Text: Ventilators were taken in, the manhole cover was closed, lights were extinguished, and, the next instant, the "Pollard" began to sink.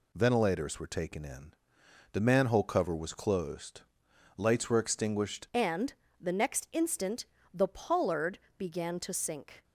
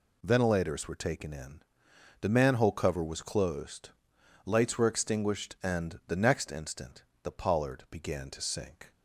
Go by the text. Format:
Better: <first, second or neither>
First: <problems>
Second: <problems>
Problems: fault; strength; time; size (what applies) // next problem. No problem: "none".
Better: second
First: changes voice at "and"; from 5.5 s on; 4.1 s long // pauses between "Pollard" and "began"; slight; at 8.3 s; 0.18 s long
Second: none